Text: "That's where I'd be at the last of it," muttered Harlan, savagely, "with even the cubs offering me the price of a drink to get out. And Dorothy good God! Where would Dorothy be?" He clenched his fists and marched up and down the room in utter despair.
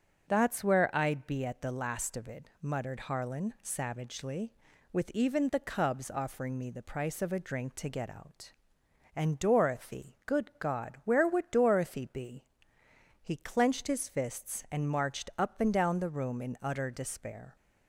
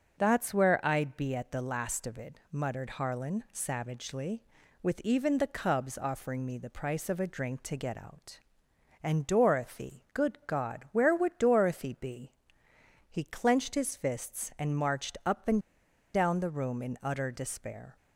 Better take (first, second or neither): first